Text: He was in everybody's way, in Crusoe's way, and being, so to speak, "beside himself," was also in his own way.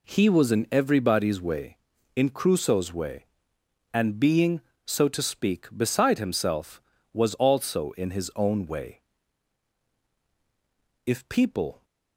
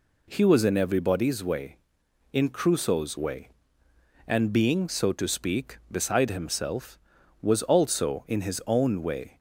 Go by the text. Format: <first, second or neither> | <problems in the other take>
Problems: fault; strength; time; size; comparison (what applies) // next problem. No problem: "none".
second | goes on to say "If people"; noticeable; from 11.0 s on; 0.78 s long